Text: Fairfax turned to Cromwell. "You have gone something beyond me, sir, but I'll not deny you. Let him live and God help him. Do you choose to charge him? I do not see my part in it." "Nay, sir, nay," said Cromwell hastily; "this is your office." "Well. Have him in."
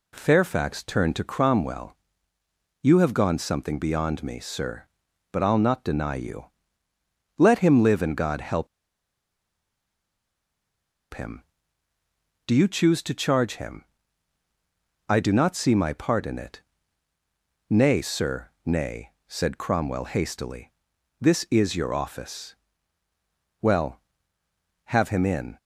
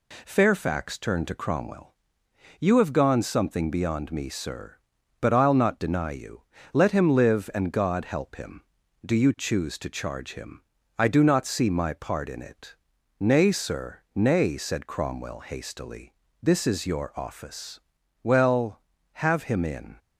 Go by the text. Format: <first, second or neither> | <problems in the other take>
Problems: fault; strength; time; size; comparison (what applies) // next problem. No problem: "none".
second | pauses between "help" and "him"; strong; at 8.6 s; 2.4 s long